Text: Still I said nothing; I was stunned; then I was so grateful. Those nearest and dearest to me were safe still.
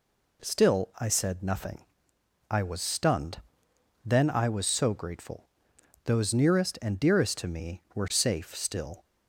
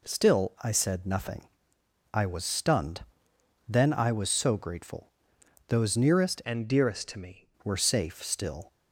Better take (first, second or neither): first